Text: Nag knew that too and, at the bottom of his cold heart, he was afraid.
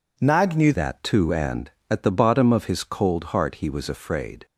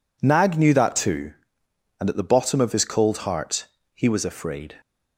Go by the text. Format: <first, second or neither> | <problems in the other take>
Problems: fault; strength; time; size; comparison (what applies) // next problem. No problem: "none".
second | changes voice at "that"; from 0.7 s on; 3.7 s long